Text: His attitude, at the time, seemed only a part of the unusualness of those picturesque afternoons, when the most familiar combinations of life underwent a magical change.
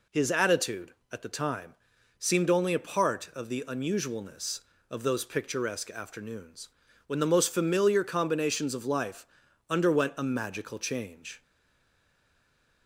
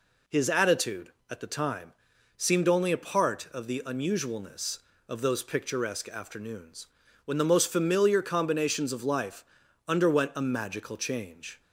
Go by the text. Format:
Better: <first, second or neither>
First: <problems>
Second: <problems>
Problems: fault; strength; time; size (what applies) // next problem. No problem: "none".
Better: second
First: pauses between "life" and "underwent"; at 9.2 s; 0.44 s long // stays silent after the last word; noticeable; from 11.4 s on; 1.4 s long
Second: pauses between "life" and "underwent"; at 9.4 s; 0.44 s long